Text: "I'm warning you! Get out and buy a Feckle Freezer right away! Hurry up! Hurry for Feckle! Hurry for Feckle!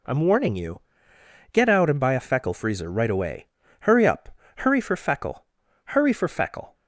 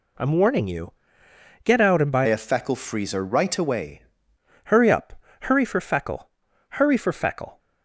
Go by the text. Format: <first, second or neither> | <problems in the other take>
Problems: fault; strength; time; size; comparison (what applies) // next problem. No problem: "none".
first | changes voice from "a" to "away"; from 2.2 to 4.0 s; 1.8 s long